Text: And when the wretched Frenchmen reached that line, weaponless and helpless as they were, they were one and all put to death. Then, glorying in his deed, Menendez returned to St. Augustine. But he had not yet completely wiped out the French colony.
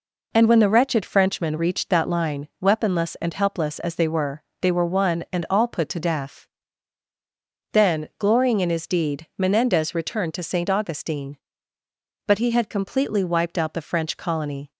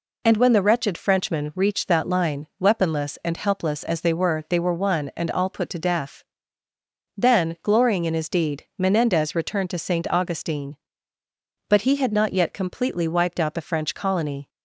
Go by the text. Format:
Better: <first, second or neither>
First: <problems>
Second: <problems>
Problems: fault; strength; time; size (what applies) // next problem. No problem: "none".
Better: second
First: skips "not yet"; at 12.6 s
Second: none